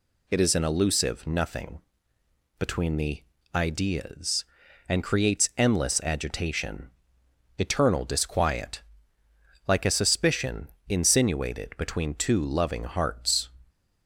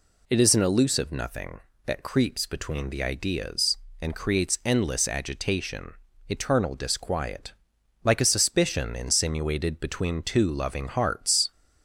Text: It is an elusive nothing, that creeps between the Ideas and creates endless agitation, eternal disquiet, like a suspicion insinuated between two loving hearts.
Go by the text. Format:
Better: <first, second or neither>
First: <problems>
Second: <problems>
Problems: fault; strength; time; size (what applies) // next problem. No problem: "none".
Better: second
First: skips "that creeps"; at 2.1 s // pauses between "the" and "Ideas"; slight; at 3.2 s; 0.32 s long // pauses between "suspicion" and "insinuated"; slight; at 10.6 s; 0.22 s long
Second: none